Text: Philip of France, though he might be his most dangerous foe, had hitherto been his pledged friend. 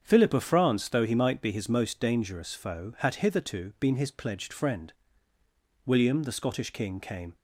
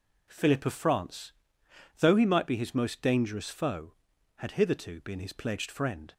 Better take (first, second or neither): second